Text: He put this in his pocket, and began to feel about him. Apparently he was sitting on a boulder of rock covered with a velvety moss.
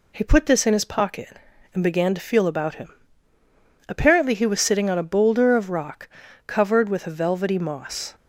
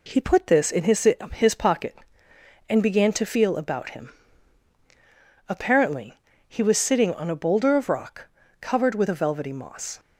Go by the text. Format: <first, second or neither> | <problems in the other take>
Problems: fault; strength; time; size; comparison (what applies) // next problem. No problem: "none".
first | says "his" twice; at 1.3 s // pauses between "Apparently" and "he"; slight; at 6.1 s; 0.32 s long // pauses between "rock" and "covered"; slight; at 8.2 s; 0.32 s long; also in the first